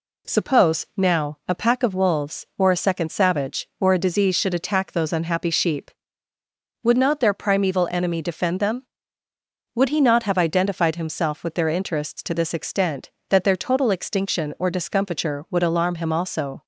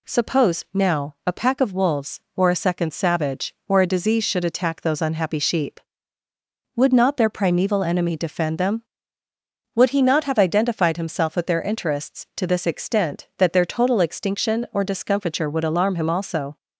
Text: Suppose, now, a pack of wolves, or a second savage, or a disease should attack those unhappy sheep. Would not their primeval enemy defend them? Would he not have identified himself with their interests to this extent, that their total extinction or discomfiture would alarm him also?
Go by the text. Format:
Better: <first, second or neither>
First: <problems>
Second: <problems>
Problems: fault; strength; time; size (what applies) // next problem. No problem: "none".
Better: neither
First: none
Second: none